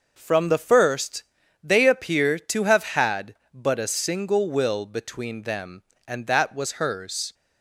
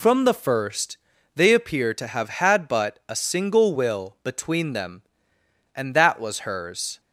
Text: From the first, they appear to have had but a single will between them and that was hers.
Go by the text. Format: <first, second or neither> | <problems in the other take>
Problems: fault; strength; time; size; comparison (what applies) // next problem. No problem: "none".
neither | none